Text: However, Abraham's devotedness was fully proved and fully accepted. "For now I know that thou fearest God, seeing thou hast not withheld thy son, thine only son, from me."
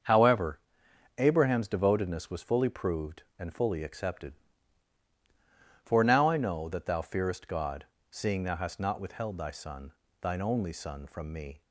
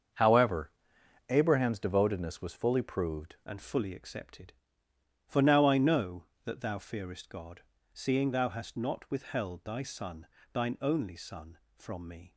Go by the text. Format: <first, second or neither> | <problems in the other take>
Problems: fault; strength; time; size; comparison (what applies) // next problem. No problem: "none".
first | starts louder than the rest; until 1.7 s; 7 dB; also in the first // changes voice at "and"; from 3.4 s on; 8.9 s long